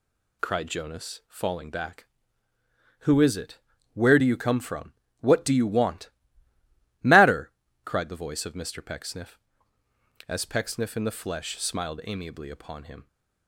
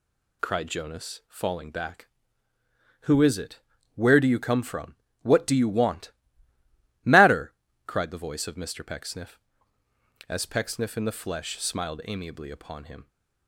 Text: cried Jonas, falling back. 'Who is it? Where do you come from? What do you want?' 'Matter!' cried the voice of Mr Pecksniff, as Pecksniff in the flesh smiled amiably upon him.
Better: neither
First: none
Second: none

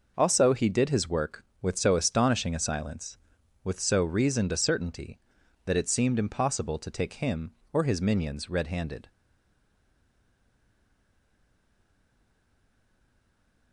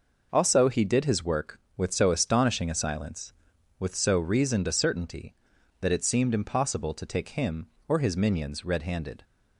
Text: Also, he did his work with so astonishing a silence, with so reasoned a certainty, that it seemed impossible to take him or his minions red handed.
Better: second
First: stays silent after the last word; strong; from 9.0 s on; 4.7 s long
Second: none

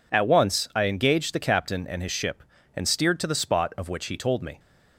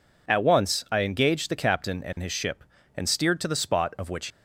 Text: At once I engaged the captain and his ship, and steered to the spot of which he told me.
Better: first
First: none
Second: stops before "he told me"; at 4.2 s

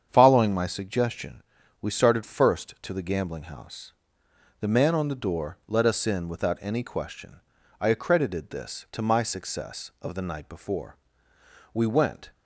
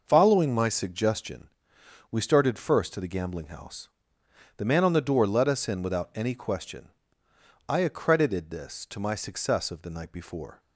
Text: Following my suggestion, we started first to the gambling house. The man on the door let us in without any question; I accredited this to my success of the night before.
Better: second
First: starts louder than the rest; strong; until 1.1 s; 8 dB // goes on to say "We went"; from 11.7 s on; 0.56 s long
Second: none

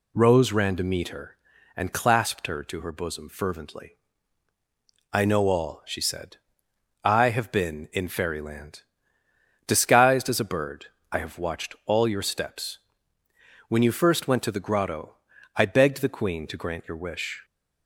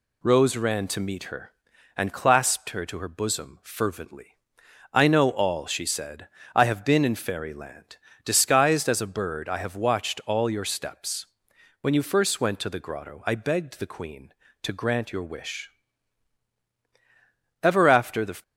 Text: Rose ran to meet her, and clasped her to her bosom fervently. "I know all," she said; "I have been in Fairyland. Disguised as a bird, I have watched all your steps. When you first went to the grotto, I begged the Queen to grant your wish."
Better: first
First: none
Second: goes on to say "Ever after the"; noticeable; from 17.6 s on; 0.80 s long

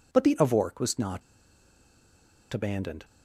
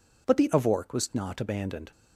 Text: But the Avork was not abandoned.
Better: second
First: pauses between "not" and "abandoned"; strong; at 1.2 s; 1.3 s long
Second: none

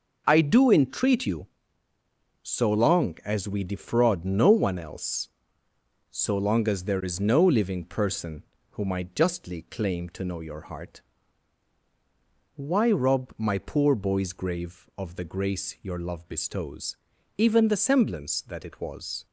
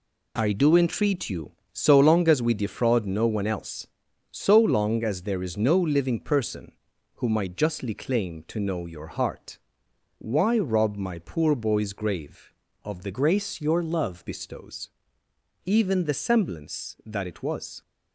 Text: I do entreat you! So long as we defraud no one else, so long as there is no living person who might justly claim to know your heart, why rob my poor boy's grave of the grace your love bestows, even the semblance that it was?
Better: first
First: none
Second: changes voice from "grace" to "love"; from 13.1 to 14.2 s; 1.1 s long

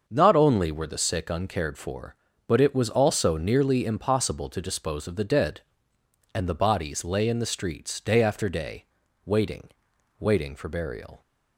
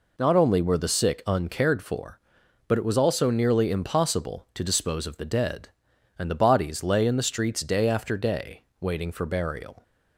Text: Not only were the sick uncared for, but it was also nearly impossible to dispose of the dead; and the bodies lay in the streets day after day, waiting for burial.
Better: second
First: starts louder than the rest; until 1.0 s; 6.5 dB // says "waiting" twice; at 10.1 s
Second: none

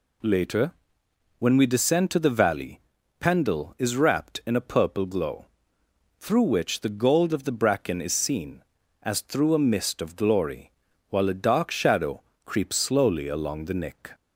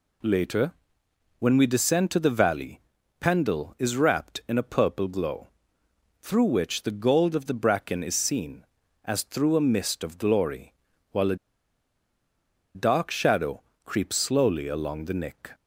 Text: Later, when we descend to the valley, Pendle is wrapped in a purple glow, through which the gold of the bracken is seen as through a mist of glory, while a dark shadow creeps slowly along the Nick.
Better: first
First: pauses between "shadow" and "creeps"; slight; at 12.2 s; 0.22 s long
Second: pauses between "a" and "dark"; strong; at 11.3 s; 1.3 s long // pauses between "shadow" and "creeps"; slight; at 13.6 s; 0.22 s long

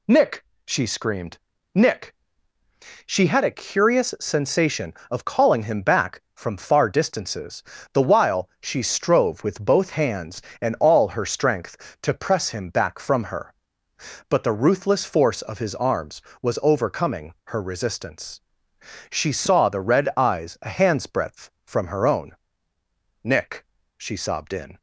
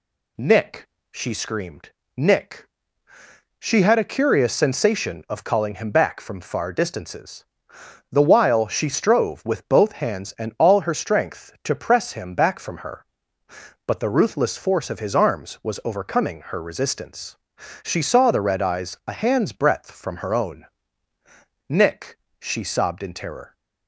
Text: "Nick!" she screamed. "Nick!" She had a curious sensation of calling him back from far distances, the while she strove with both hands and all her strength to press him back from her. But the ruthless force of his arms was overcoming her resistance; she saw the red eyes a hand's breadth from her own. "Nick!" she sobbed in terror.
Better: second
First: stops before "terror"; at 24.7 s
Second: none

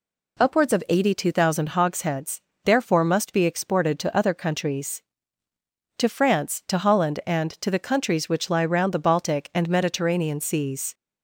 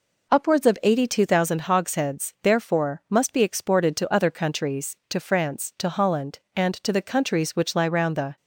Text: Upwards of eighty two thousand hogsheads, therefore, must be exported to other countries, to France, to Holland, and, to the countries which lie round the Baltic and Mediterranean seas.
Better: first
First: none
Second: stops before "Baltic and Mediterranean seas"; at 8.3 s

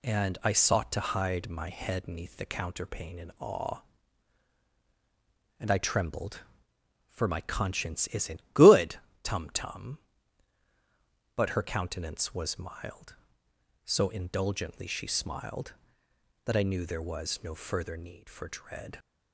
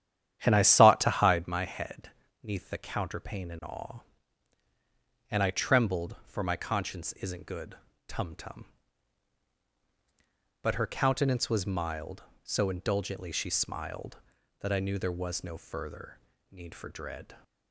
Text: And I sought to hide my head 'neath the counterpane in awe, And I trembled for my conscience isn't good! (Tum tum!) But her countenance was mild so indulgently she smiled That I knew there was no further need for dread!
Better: first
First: none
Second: starts louder than the rest; strong; until 1.5 s; 10 dB // pauses between "head" and "neath"; slight; at 2.1 s; 0.32 s long // pauses between "further" and "need"; slight; at 16.1 s; 0.34 s long

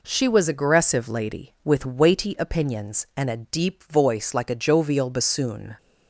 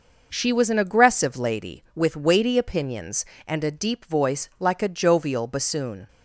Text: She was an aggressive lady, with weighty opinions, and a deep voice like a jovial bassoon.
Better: second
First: skips "an"; at 0.4 s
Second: none

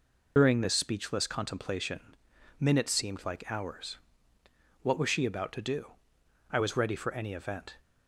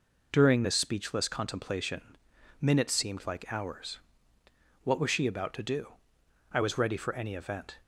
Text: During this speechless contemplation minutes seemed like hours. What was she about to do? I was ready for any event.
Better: second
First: loses the start of "During"; at 0.3 s; 55 ms // pauses between "contemplation" and "minutes"; at 2.1 s; 0.44 s long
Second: pauses between "contemplation" and "minutes"; at 2.1 s; 0.44 s long

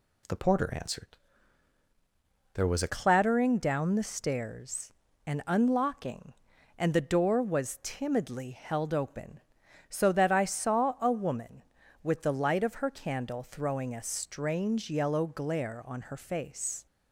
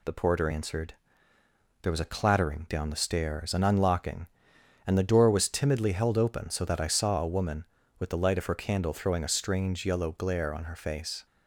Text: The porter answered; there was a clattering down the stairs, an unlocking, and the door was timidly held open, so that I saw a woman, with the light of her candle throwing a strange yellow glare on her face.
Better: second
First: changes voice at "clattering"; from 2.8 s on; 14.0 s long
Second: none

